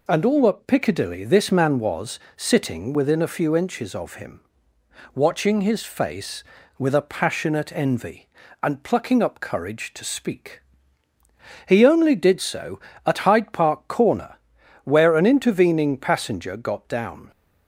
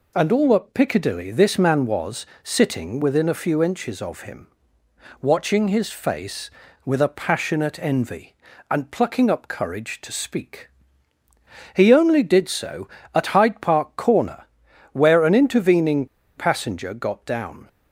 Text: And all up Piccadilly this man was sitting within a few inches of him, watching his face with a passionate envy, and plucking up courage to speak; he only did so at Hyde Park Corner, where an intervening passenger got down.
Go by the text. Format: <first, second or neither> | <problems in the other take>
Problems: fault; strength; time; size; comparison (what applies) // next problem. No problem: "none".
first | pauses between "was" and "sitting"; slight; at 2.2 s; 0.18 s long; slight in the first // pauses between "intervening" and "passenger"; slight; at 16.0 s; 0.31 s long